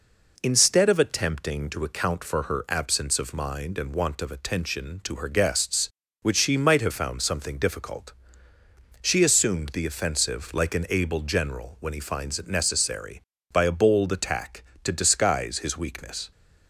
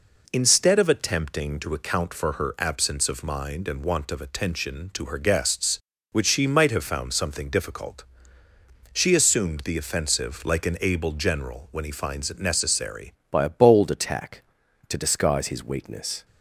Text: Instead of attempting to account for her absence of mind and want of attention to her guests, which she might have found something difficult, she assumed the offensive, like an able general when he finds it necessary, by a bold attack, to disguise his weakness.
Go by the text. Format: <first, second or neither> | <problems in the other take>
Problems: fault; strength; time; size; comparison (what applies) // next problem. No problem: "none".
first | changes voice at "by"; from 13.2 s on; 3.0 s long